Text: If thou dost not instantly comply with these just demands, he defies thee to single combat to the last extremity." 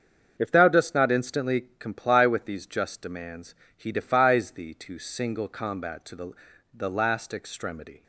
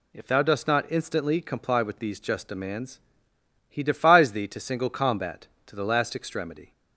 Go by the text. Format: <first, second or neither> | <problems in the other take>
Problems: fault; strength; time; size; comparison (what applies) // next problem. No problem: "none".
second | starts louder than the rest; until 1.3 s; 7 dB // says "the" twice; at 6.7 s